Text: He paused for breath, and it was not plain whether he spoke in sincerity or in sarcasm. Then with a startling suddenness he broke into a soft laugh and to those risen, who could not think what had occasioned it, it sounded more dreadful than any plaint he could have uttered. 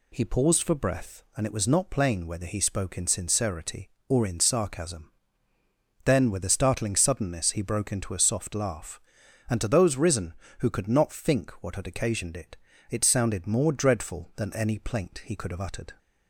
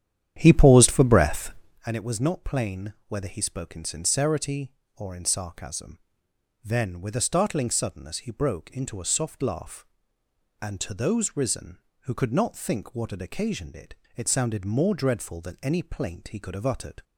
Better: first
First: none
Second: starts louder than the rest; strong; until 1.9 s; 10 dB

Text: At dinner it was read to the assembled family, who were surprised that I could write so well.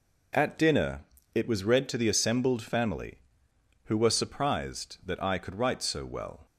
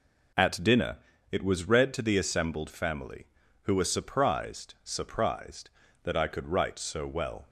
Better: first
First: pauses between "dinner" and "it"; slight; at 1.0 s; 0.29 s long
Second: pauses between "dinner" and "it"; slight; at 0.9 s; 0.34 s long // says "surprised" twice; at 4.8 s

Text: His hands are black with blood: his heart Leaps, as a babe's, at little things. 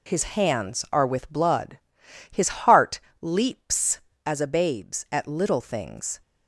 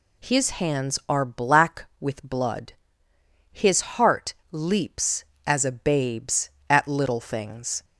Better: second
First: skips "black"; at 1.0 s // pauses between "heart" and "Leaps"; slight; at 3.0 s; 0.20 s long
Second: pauses between "heart" and "Leaps"; slight; at 4.3 s; 0.16 s long

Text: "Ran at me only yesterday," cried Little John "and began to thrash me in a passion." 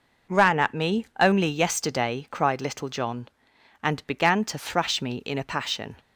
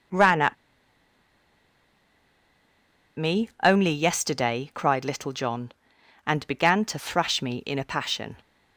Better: first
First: none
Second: pauses between "at" and "me"; strong; at 0.5 s; 2.6 s long

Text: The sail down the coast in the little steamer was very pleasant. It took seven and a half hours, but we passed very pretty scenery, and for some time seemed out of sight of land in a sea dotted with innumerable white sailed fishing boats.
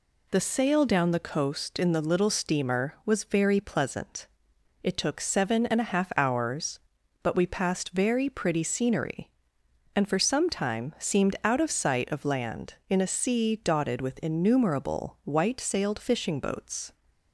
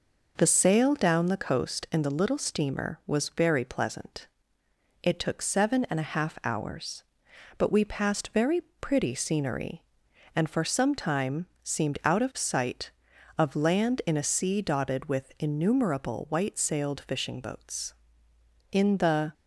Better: first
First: none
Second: pauses between "very" and "pretty"; slight; at 8.6 s; 0.22 s long // pauses between "time" and "seemed"; slight; at 11.4 s; 0.16 s long // goes on to say "In the"; noticeable; from 18.7 s on; 0.62 s long

